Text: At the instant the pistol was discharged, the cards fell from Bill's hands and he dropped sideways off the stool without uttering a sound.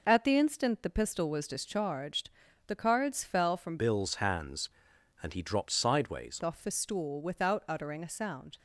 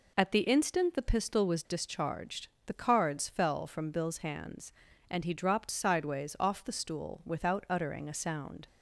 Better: second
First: changes voice from "Bill's" to "sideways"; from 3.7 to 6.3 s; 2.6 s long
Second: none

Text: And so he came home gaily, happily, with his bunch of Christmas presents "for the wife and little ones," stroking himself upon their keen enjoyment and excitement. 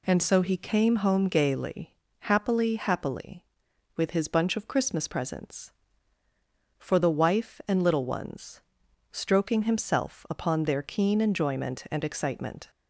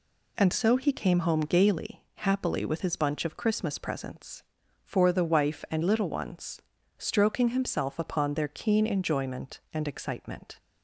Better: second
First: says "happily" twice; at 2.7 s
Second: none

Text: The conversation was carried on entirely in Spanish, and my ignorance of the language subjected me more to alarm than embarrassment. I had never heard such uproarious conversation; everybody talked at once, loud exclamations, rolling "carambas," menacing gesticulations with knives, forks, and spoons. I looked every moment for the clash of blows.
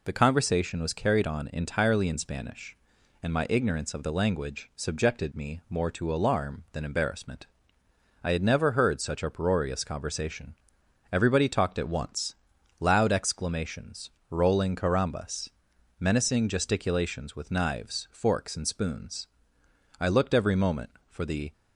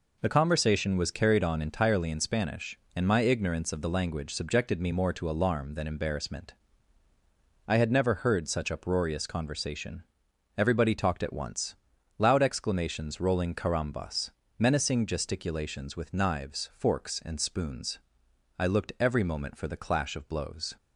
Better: second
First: stops before "clash of blows"; at 21.5 s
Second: none

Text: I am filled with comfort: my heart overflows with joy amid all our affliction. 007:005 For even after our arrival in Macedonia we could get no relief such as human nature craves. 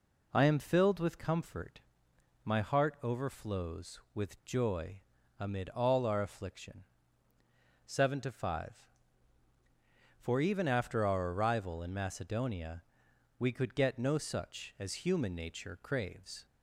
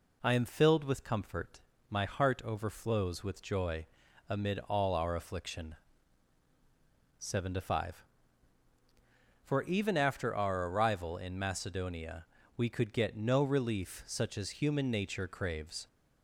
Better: second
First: pauses between "joy" and "amid"; at 4.9 s; 0.40 s long // pauses between "Macedonia" and "we"; noticeable; at 12.8 s; 0.58 s long // skips "relief"; at 14.1 s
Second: pauses between "joy" and "amid"; noticeable; at 3.8 s; 0.46 s long // pauses between "Macedonia" and "we"; slight; at 12.2 s; 0.32 s long

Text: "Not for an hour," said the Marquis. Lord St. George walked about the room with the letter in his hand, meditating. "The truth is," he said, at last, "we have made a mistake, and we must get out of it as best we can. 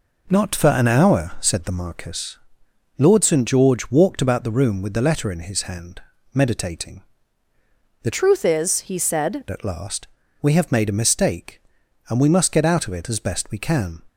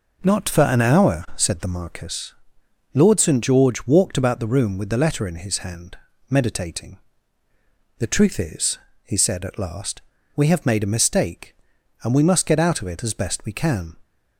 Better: second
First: changes voice from "truth" to "said"; from 8.1 to 9.4 s; 1.3 s long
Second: none

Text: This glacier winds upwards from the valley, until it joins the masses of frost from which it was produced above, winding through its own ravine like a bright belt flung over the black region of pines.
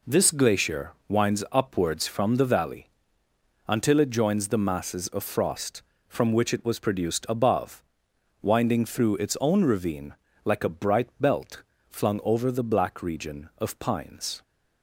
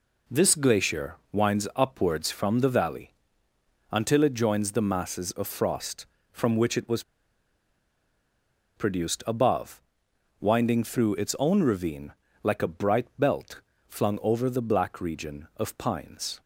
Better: first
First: pauses between "glacier" and "winds"; slight; at 0.9 s; 0.16 s long // pauses between "ravine" and "like"; slight; at 10.1 s; 0.32 s long // pauses between "belt" and "flung"; slight; at 11.6 s; 0.26 s long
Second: pauses between "glacier" and "winds"; slight; at 1.1 s; 0.16 s long // pauses between "was" and "produced"; strong; at 7.0 s; 1.7 s long // pauses between "ravine" and "like"; slight; at 12.1 s; 0.32 s long // pauses between "belt" and "flung"; slight; at 13.6 s; 0.26 s long

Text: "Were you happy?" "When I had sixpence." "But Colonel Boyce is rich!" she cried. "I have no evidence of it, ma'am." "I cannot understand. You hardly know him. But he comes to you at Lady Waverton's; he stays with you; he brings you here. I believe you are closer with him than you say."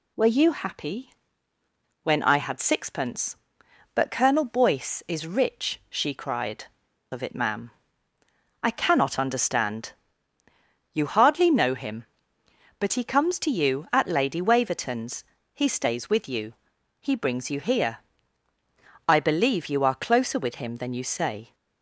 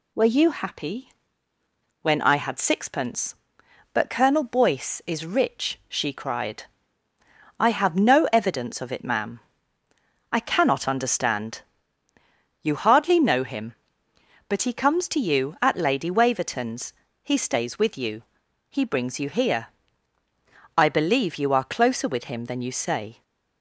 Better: second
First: skips "I have no evidence"; at 6.8 s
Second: none

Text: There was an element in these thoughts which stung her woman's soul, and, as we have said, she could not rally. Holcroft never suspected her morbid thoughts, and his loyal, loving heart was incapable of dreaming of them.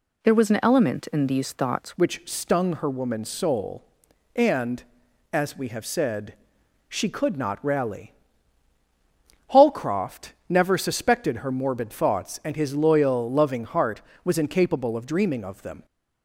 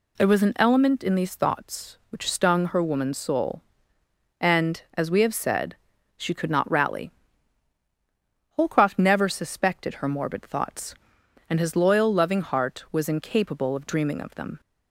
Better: second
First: changes voice at "which"; from 1.9 s on; 13.9 s long // pauses between "Holcroft" and "never"; slight; at 10.3 s; 0.16 s long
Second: none

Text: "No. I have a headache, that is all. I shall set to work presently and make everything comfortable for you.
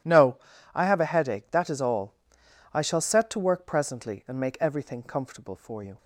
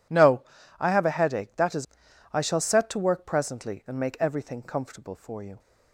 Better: first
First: none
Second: skips "all"; at 2.0 s

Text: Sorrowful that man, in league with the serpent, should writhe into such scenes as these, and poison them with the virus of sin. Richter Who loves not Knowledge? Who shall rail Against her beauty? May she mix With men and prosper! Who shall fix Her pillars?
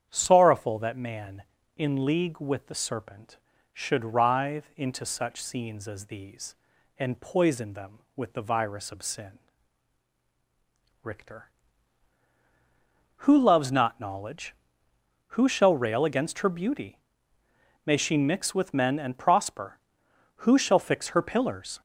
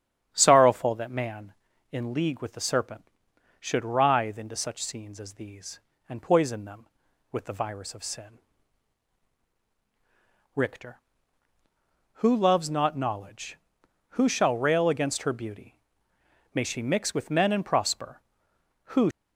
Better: first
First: starts louder than the rest; strong; until 1.1 s; 8.5 dB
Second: starts louder than the rest; strong; until 1.3 s; 9.5 dB // stops before "shall fix Her pillars"; at 19.1 s

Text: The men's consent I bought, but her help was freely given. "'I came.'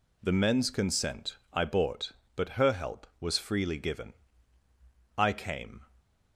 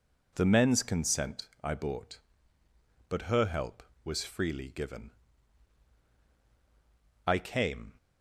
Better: neither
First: pauses between "consent" and "I"; slight; at 1.3 s; 0.16 s long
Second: pauses between "consent" and "I"; slight; at 1.4 s; 0.16 s long

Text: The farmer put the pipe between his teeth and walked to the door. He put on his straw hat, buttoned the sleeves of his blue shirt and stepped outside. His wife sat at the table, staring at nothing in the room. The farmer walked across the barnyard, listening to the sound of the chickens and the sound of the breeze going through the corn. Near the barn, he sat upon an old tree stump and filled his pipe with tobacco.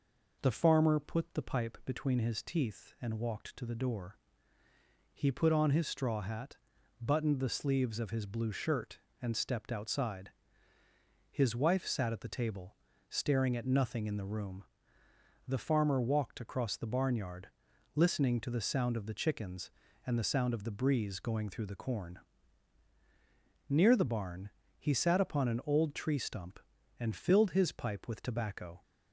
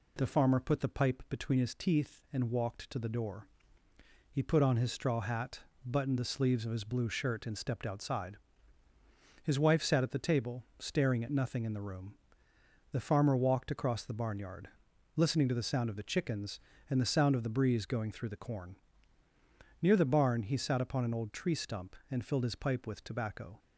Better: neither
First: none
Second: none

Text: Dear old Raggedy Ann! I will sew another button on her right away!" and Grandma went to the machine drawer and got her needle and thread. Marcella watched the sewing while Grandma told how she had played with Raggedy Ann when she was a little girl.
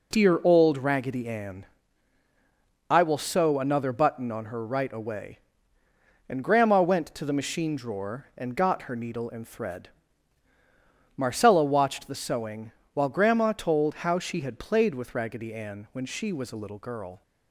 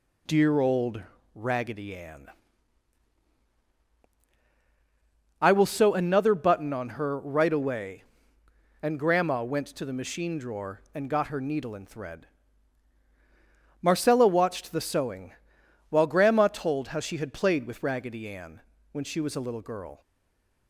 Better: first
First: pauses between "sewing" and "while"; slight; at 12.7 s; 0.20 s long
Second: pauses between "old" and "Raggedy"; slight; at 1.0 s; 0.34 s long // pauses between "sewing" and "while"; noticeable; at 15.3 s; 0.60 s long // pauses between "Ann" and "when"; slight; at 18.5 s; 0.32 s long // stays silent after the last word; slight; from 20.0 s on; 0.6 s long

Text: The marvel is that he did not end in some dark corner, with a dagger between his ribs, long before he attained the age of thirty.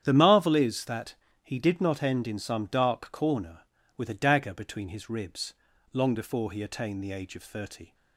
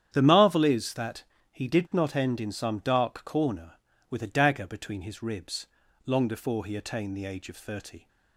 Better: neither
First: starts louder than the rest; strong; until 1.0 s; 9.5 dB // pauses between "that" and "he"; slight; at 1.1 s; 0.30 s long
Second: starts louder than the rest; strong; until 1.1 s; 9.5 dB // pauses between "that" and "he"; slight; at 1.2 s; 0.30 s long

